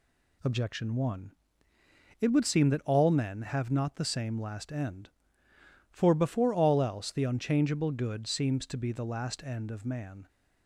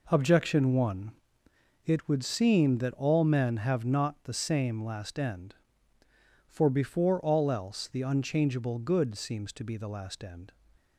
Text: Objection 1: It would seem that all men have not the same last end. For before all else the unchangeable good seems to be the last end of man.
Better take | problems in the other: first | stops before "of man"; at 10.7 s

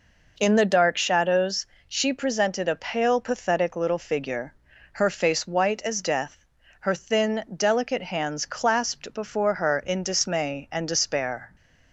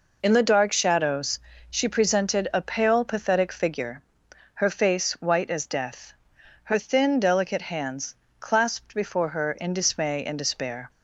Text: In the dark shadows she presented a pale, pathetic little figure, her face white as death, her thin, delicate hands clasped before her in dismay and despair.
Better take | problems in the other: first | pauses between "shadows" and "she"; slight; at 1.3 s; 0.32 s long; slight in the first // skips "little"; at 3.5 s // pauses between "hands" and "clasped"; slight; at 8.1 s; 0.26 s long

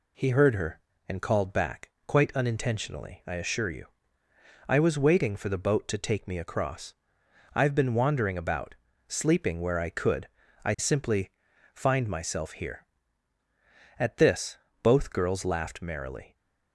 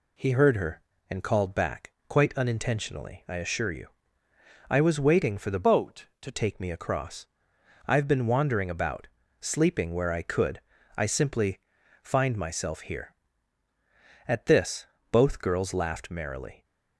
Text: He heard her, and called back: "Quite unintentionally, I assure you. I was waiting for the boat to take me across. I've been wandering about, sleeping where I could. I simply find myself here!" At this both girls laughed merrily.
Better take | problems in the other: first | changes voice from "boat" to "to"; from 5.6 to 6.3 s; 0.7 s long // pauses between "simply" and "find"; at 11.6 s; 0.42 s long; also in the first // pauses between "this" and "both"; slight; at 14.8 s; 0.24 s long; slight in the first

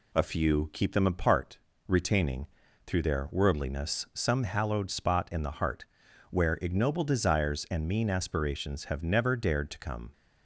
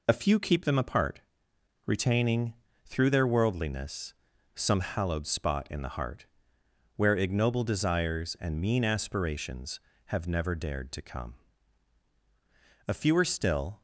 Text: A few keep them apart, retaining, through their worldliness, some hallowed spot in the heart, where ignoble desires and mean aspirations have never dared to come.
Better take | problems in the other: first | goes on to say "A fewer still"; noticeable; from 12.8 s on; 0.94 s long

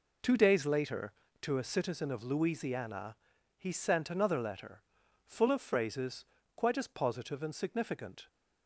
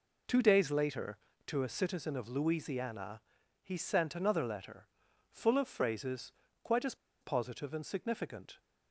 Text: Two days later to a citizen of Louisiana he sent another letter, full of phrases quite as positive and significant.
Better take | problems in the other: first | pauses between "Louisiana" and "he"; at 3.2 s; 0.42 s long; also in the first // pauses between "phrases" and "quite"; slight; at 6.3 s; 0.32 s long; slight in the first // pauses between "as" and "positive"; slight; at 6.9 s; 0.26 s long

